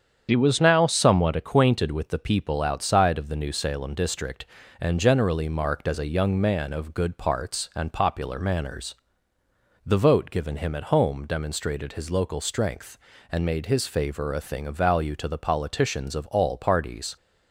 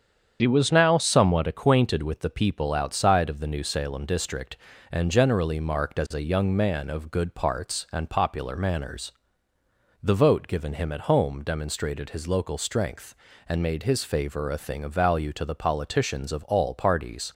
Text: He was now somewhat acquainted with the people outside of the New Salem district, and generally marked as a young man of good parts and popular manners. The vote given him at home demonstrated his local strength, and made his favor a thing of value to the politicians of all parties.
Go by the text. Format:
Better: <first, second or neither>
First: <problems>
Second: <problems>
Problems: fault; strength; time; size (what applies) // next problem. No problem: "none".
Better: neither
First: starts louder than the rest; strong; until 1.3 s; 8 dB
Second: starts louder than the rest; strong; until 1.4 s; 8 dB